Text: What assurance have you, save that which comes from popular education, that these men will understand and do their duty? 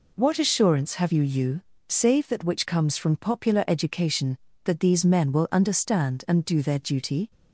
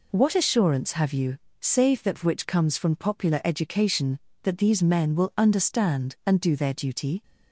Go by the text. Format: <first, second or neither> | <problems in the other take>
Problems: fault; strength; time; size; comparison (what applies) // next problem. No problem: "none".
second | says "you" twice; at 1.2 s